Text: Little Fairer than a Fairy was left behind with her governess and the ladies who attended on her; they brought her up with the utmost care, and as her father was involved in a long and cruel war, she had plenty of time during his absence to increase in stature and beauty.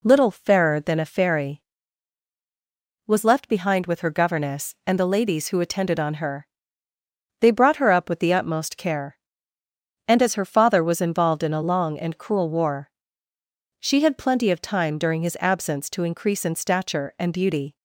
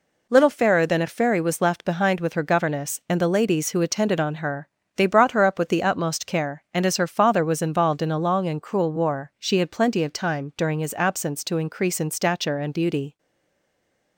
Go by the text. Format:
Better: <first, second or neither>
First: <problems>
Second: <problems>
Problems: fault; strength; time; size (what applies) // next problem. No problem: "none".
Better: first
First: none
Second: stays silent after the last word; from 13.1 s on; 1.0 s long